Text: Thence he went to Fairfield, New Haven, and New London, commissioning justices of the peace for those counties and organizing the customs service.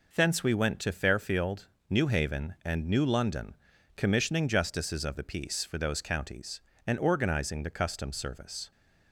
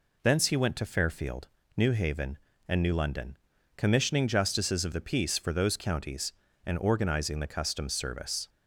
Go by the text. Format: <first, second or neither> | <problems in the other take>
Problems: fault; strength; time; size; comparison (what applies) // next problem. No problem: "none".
second | says "we" for "he"; at 0.4 s